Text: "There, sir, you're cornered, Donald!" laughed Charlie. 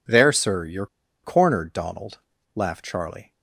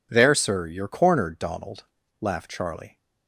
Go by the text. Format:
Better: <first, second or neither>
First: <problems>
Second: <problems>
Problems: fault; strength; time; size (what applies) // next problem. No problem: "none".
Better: second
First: pauses between "you're" and "cornered"; at 0.8 s; 0.37 s long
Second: none